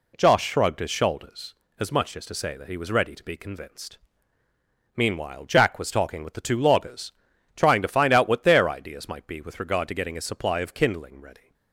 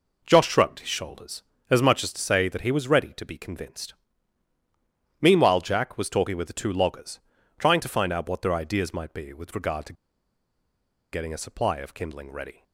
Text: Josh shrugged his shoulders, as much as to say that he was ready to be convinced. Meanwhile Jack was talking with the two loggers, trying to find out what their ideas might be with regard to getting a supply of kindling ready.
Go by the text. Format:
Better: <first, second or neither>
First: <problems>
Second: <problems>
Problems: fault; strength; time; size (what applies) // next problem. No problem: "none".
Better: first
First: none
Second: pauses between "to" and "getting"; at 9.9 s; 1.1 s long